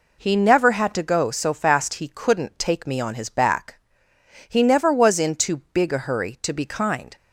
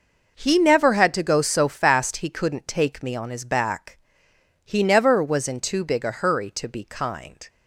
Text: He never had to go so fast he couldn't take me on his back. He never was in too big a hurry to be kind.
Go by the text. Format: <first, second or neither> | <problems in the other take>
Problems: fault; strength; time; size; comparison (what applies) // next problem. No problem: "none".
neither | none